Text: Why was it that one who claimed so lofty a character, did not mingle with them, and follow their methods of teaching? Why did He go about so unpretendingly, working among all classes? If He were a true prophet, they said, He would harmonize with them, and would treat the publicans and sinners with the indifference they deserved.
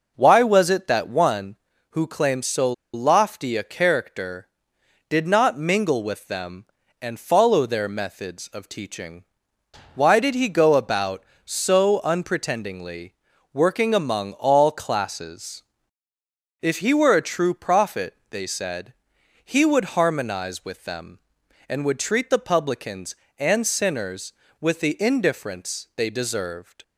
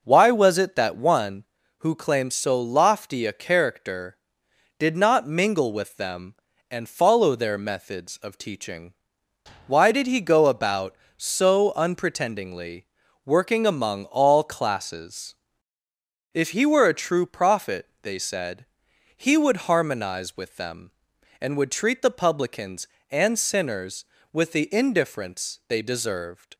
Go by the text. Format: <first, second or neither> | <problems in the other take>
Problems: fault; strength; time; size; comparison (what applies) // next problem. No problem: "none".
second | pauses between "so" and "lofty"; slight; at 2.7 s; 0.21 s long